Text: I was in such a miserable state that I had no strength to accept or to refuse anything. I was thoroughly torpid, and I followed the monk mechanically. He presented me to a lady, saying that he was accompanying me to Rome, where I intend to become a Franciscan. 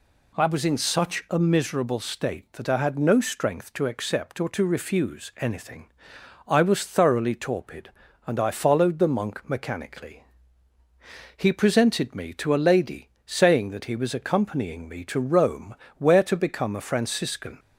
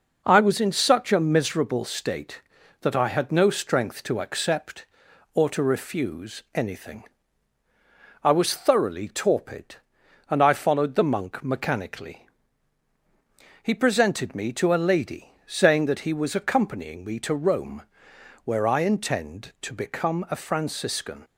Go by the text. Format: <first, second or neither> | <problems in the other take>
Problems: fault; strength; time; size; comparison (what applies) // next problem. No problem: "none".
second | skips "I intend"; at 16.2 s